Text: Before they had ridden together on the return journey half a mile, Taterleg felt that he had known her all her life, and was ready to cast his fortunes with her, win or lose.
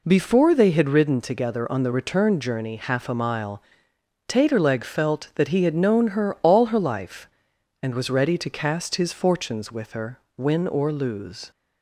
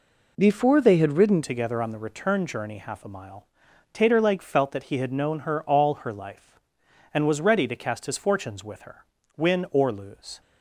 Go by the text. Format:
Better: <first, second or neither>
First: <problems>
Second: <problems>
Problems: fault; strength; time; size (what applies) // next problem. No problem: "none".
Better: first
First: none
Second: changes voice at "together"; from 1.4 s on; 9.0 s long